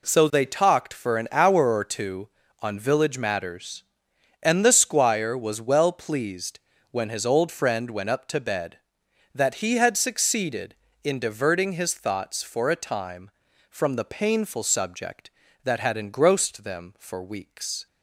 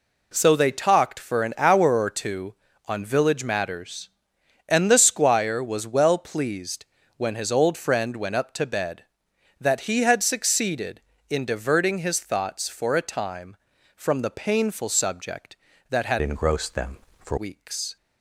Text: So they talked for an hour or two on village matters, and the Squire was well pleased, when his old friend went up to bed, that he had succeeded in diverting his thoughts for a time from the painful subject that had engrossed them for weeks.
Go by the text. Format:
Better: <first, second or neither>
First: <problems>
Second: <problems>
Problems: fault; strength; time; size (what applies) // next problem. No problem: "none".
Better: first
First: none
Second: changes voice from "engrossed" to "for"; from 16.2 to 17.3 s; 1.1 s long